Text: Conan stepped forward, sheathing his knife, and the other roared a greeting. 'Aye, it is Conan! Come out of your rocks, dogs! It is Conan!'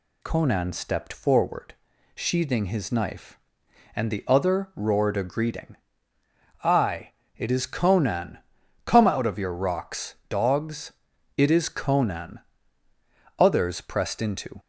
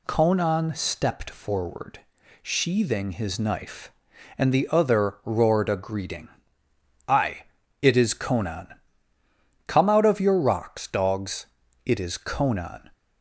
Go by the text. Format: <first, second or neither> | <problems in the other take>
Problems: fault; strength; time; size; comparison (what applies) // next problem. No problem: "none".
second | goes on to say "Others pressed into"; noticeable; from 13.3 s on; 1.2 s long